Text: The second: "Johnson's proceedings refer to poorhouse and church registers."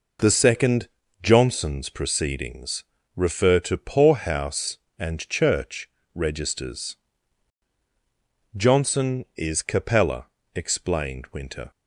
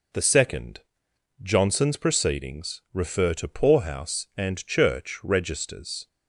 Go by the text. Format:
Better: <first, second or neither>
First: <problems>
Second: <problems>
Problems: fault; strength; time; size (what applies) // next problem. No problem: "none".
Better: second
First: pauses between "proceedings" and "refer"; slight; at 2.8 s; 0.32 s long // pauses between "church" and "registers"; slight; at 5.8 s; 0.26 s long // goes on to say "Johnson is Capella explained Winter"; strong; from 8.5 s on; 3.1 s long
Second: none